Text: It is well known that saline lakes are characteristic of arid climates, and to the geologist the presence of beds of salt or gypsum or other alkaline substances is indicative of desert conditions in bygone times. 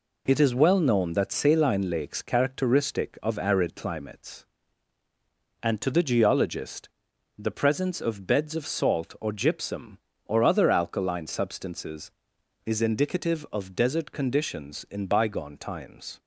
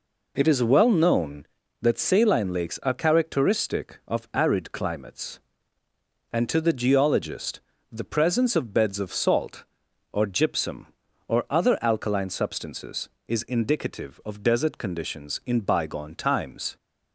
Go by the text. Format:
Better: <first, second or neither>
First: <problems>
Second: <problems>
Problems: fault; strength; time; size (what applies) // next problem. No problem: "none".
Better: second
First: skips "are"; at 2.2 s // pauses between "geologist" and "the"; noticeable; at 6.8 s; 0.50 s long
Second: pauses between "geologist" and "the"; slight; at 7.6 s; 0.30 s long